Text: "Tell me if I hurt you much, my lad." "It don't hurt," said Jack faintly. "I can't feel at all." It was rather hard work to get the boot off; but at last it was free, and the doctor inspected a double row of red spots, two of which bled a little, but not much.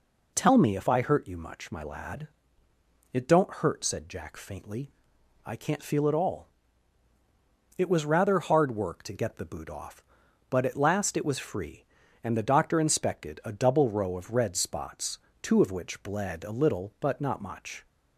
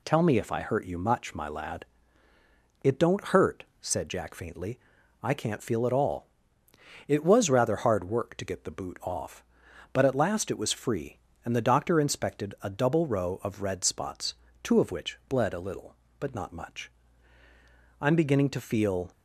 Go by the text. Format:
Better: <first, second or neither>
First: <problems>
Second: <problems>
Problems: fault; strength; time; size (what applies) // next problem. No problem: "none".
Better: first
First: none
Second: goes on to say "I'm beginning to feel"; noticeable; from 18.0 s on; 1.0 s long